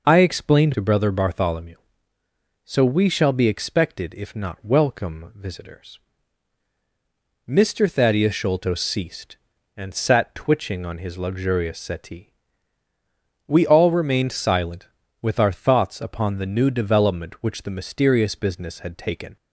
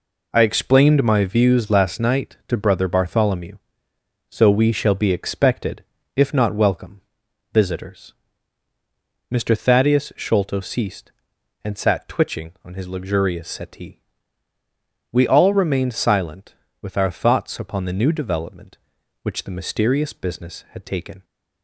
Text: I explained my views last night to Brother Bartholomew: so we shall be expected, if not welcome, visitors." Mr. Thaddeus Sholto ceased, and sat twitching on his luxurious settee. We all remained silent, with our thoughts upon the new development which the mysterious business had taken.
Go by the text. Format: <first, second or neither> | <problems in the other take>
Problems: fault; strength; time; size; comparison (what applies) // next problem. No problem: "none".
second | skips "my views last night"; at 0.7 s